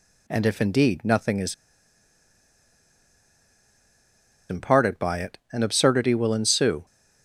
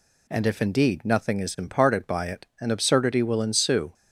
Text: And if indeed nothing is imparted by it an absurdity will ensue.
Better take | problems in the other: second | pauses between "is" and "imparted"; strong; at 1.5 s; 2.9 s long

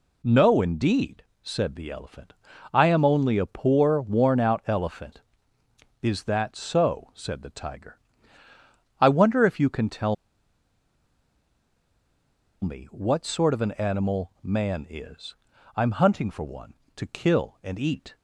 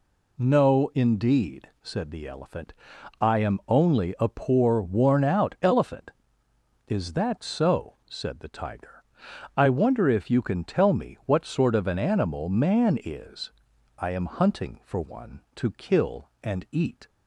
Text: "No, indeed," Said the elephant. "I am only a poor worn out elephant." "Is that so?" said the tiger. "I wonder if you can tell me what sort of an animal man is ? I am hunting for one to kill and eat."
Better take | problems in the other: second | pauses between "tell" and "me"; strong; at 10.1 s; 2.4 s long

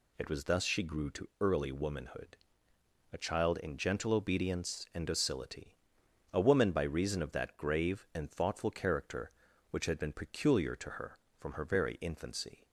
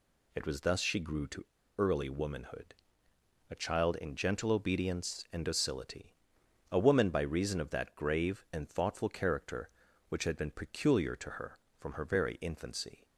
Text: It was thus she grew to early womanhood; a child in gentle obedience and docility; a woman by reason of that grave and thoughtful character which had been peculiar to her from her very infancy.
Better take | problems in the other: first | pauses between "to" and "early"; slight; at 1.4 s; 0.32 s long

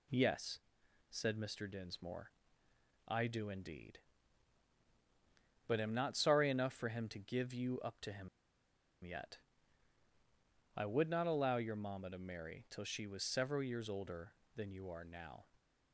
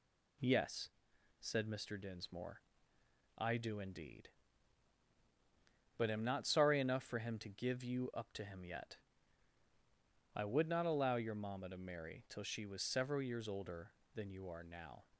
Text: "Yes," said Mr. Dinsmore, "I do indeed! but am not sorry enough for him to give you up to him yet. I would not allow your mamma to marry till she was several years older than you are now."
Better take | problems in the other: second | pauses between "him" and "yet"; noticeable; at 8.2 s; 0.76 s long

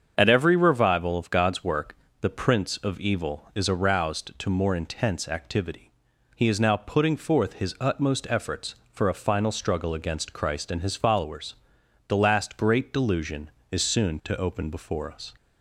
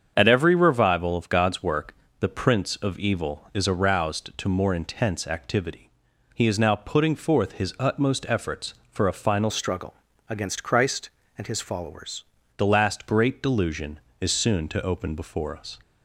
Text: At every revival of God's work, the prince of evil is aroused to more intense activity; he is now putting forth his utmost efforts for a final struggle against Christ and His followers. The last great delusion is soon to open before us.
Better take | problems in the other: first | starts louder than the rest; strong; until 1.1 s; 7.5 dB; strong in the first // changes voice from "struggle" to "followers"; from 9.4 to 12.2 s; 2.8 s long // pauses between "struggle" and "against"; slight; at 9.9 s; 0.34 s long

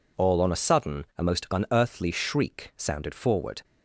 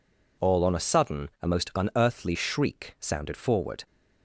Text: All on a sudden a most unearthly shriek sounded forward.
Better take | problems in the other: neither | none

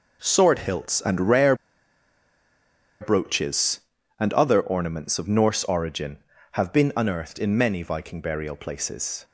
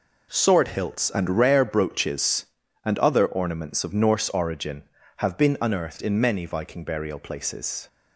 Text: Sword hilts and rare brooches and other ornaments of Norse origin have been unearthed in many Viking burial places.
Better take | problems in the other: second | pauses between "rare" and "brooches"; strong; at 1.5 s; 1.4 s long

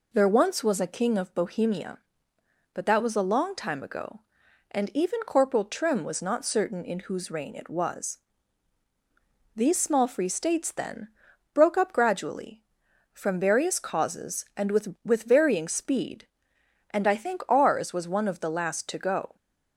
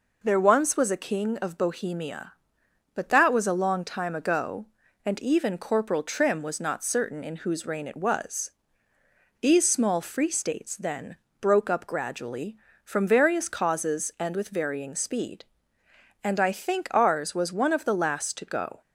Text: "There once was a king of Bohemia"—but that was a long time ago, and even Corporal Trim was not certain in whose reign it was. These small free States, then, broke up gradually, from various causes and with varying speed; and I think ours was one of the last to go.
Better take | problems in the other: second | says "with" twice; at 15.0 s

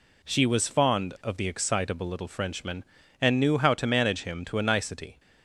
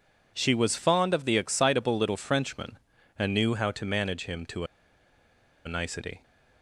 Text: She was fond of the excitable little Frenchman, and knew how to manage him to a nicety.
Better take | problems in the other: first | pauses between "to" and "a"; at 4.6 s; 0.99 s long

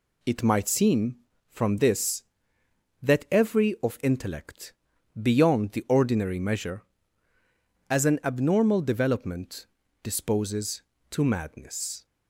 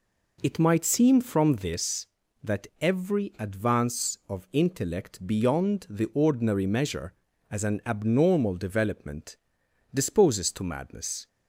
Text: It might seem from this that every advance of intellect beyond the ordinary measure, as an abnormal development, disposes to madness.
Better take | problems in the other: second | skips "advance"; at 3.7 s // pauses between "intellect" and "beyond"; noticeable; at 4.7 s; 0.46 s long

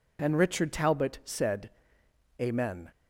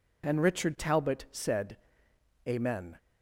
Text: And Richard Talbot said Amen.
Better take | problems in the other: neither | pauses between "said" and "Amen"; noticeable; the same in both

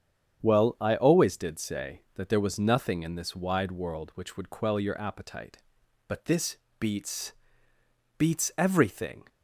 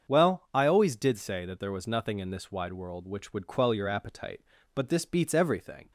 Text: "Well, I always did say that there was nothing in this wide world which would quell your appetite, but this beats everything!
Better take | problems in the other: second | starts louder than the rest; strong; until 1.4 s; 8 dB; also in the second // pauses between "this" and "beats"; slight; at 6.5 s; 0.22 s long // says "beats" twice; at 8.1 s

